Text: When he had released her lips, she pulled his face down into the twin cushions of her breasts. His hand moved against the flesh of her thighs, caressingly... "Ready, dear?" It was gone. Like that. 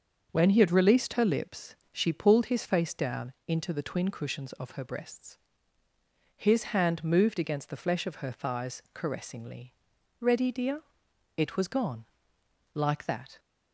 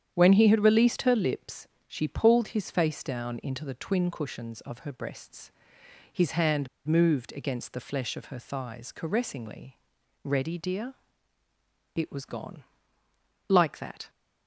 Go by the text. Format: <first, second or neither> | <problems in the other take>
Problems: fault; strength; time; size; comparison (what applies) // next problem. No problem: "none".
first | starts louder than the rest; strong; until 1.1 s; 9 dB; also in the first // pauses between "hand" and "moved"; slight; at 6.6 s; 0.19 s long